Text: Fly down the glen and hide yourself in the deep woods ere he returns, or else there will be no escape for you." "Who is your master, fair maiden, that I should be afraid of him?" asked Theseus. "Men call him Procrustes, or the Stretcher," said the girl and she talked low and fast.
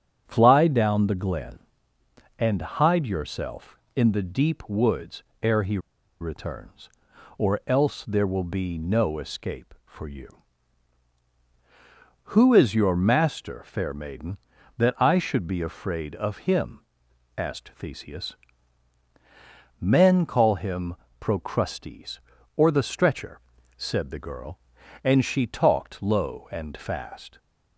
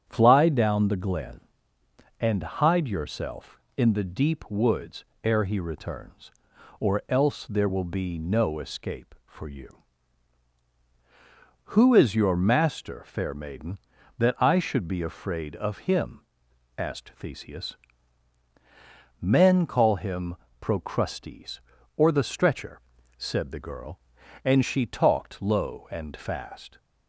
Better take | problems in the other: second | starts louder than the rest; strong; until 1.2 s; 9 dB; strong in the second // pauses between "woods" and "ere"; slight; at 5.2 s; 0.18 s long; slight in the second // pauses between "he" and "returns"; at 5.7 s; 0.42 s long // pauses between "him" and "Procrustes"; slight; at 20.9 s; 0.24 s long; slight in the second

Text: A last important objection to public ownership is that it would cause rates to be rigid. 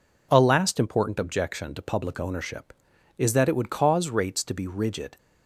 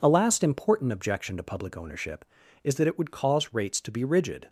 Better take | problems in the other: neither | none

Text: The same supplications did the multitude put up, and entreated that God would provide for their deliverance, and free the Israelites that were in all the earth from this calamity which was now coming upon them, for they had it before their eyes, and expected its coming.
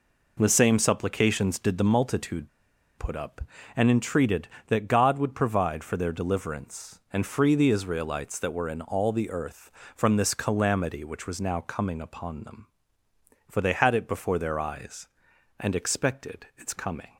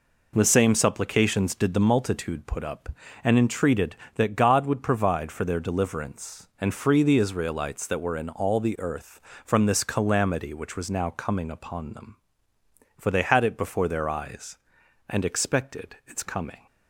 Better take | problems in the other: second | pauses between "multitude" and "put"; noticeable; at 2.4 s; 0.49 s long

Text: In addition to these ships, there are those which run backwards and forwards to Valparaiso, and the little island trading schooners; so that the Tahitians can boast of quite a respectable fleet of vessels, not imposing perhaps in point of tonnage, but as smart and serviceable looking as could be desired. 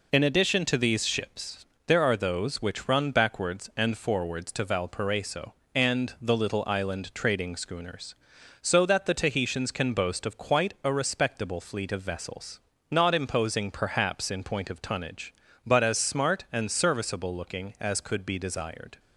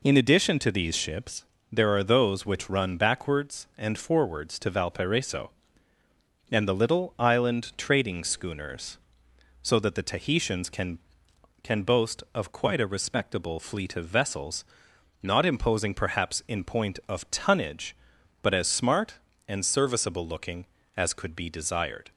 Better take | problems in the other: first | says "can" twice; at 11.6 s

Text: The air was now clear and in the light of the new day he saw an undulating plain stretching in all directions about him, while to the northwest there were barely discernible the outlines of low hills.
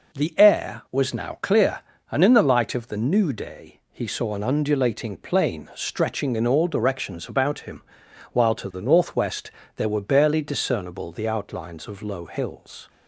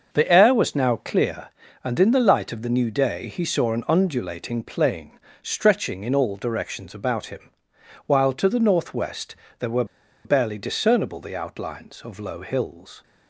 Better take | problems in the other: first | starts louder than the rest; until 1.1 s; 6.5 dB // pauses between "plain" and "stretching"; slight; at 5.1 s; 0.24 s long // pauses between "northwest" and "there"; slight; at 9.3 s; 0.22 s long; slight in the first // pauses between "were" and "barely"; at 9.8 s; 0.40 s long

